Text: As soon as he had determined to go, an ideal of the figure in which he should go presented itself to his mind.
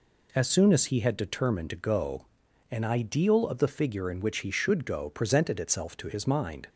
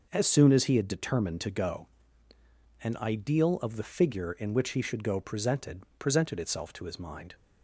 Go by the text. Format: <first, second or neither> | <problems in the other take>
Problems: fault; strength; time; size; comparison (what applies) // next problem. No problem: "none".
first | starts louder than the rest; noticeable; until 1.1 s; 6 dB // says "presented" twice; at 5.9 s